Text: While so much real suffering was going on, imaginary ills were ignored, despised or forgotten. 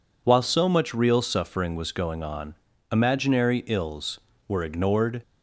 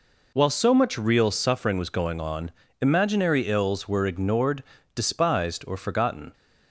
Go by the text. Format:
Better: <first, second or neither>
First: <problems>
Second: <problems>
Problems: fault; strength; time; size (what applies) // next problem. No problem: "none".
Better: second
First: stops before "despised or forgotten"; at 5.2 s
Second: none